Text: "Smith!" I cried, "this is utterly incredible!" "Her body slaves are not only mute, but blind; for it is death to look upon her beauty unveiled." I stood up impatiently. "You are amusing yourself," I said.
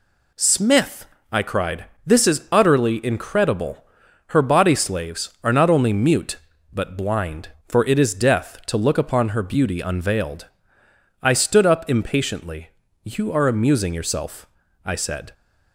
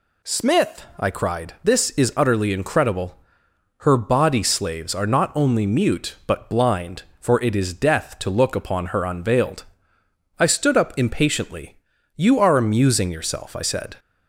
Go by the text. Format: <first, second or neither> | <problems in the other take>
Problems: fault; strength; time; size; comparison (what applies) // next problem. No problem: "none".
first | skips "beauty"; at 9.0 s